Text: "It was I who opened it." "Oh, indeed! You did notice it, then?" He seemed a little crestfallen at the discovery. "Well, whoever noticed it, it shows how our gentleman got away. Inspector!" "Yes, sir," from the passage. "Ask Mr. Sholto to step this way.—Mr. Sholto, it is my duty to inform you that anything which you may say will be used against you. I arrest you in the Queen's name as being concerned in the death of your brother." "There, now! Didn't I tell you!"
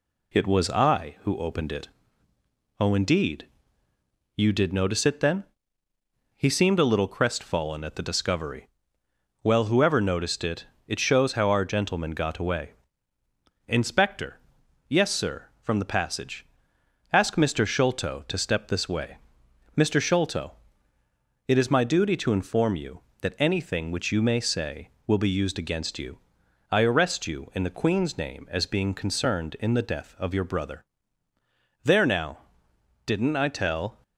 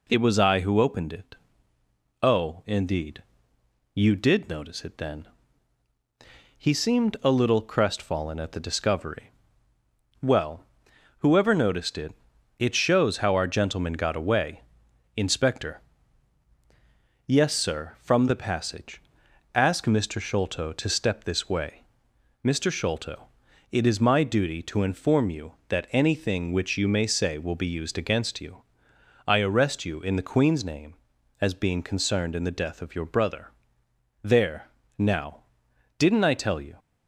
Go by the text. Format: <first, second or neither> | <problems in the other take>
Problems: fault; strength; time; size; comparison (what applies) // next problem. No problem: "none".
second | stops before "you"; at 34.0 s